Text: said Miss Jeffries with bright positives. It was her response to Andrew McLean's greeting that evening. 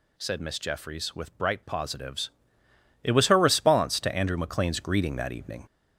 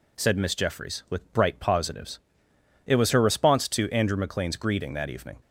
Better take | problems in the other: second | gets louder; noticeable; throughout; 4.5 dB

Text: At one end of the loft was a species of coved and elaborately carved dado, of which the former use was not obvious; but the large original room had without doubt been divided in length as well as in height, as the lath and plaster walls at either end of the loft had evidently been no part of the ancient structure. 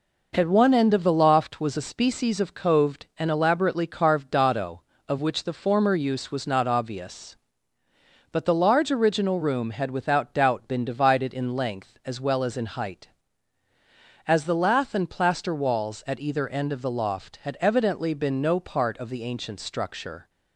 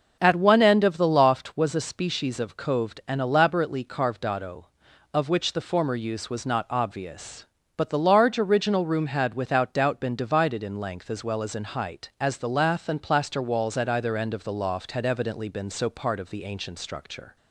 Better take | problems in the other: first | says "so" for "no"; at 15.6 s

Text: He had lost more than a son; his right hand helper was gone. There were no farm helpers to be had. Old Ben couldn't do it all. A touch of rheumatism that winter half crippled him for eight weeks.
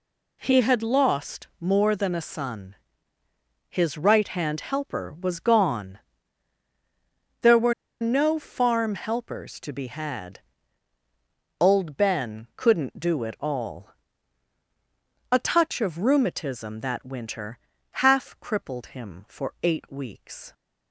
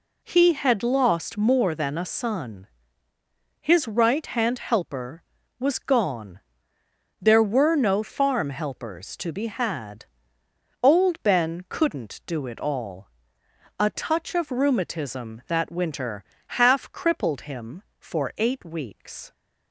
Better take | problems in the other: second | pauses between "were" and "no"; slight; at 7.7 s; 0.27 s long // pauses between "winter" and "half"; at 17.5 s; 0.44 s long; slight in the second

